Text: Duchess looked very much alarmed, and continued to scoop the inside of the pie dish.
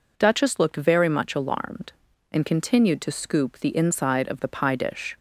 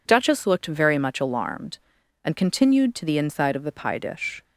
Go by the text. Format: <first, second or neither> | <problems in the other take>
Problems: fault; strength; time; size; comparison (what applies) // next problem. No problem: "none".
first | skips "scoop"; at 3.0 s